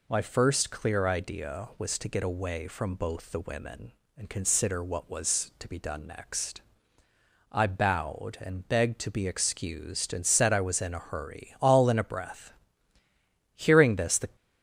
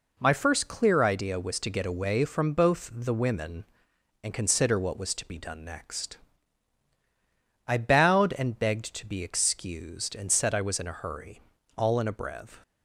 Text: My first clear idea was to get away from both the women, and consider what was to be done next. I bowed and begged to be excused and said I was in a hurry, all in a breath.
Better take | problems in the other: second | goes on to say "Hearing this the"; noticeable; from 13.5 s on; 0.80 s long

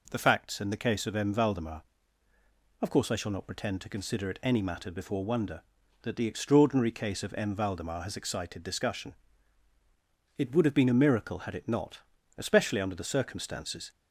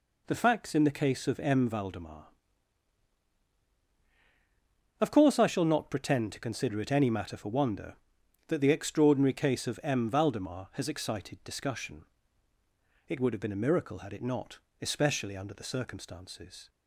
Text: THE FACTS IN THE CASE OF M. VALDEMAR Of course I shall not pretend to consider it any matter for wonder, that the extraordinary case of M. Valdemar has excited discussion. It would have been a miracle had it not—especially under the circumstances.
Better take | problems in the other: second | says "before" for "for"; at 4.9 s

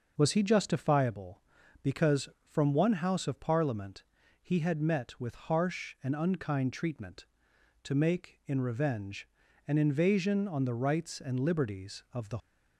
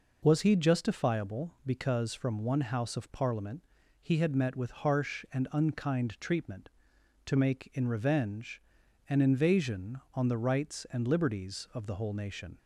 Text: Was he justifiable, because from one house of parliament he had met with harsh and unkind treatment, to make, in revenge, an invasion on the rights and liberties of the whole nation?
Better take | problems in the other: second | pauses between "parliament" and "he"; at 4.0 s; 0.40 s long; also in the second // stops before "whole nation"; at 12.3 s

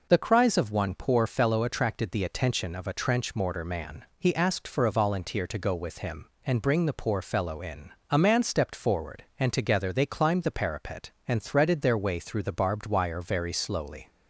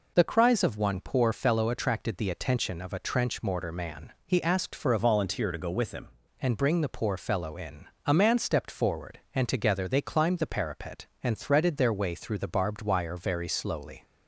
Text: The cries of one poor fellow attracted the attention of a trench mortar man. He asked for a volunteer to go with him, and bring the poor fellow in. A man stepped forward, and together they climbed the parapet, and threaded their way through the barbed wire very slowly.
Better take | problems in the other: first | changes voice from "volunteer" to "him"; from 4.9 to 6.0 s; 1.1 s long

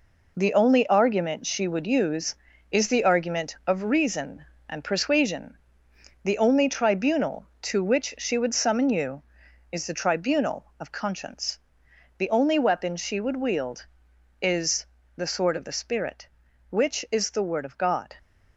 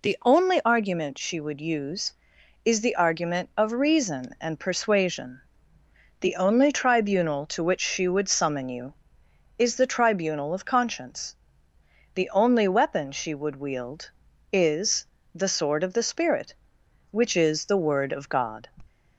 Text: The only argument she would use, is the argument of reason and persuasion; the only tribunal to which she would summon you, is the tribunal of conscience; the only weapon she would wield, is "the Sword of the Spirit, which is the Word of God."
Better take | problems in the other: second | gets quieter; strong; throughout; 7 dB // pauses between "is" and "the"; slight; at 14.8 s; 0.30 s long; slight in the second

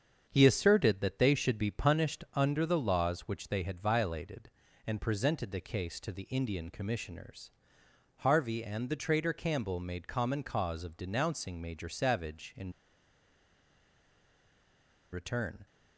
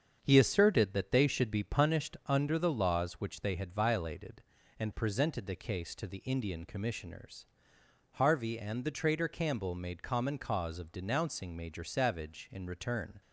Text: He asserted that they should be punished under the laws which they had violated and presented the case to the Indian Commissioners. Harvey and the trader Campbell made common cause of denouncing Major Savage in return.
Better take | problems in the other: second | starts louder than the rest; strong; until 1.3 s; 7 dB; strong in the second // pauses between "in" and "return"; strong; at 12.7 s; 2.4 s long

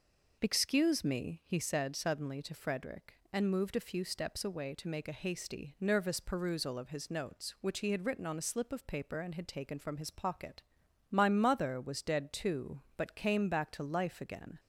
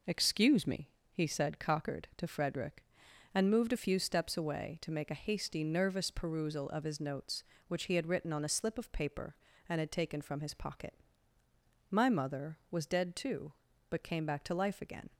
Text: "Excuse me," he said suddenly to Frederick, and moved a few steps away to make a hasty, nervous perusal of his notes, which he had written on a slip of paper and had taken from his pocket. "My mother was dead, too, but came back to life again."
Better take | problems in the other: first | says "cockered" for "suddenly"; at 1.5 s

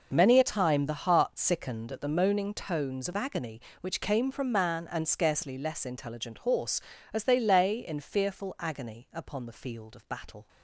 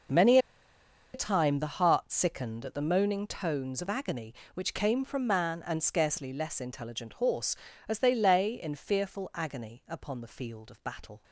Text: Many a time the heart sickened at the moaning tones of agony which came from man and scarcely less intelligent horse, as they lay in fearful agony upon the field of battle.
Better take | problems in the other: first | pauses between "Many" and "a"; noticeable; at 0.3 s; 0.74 s long

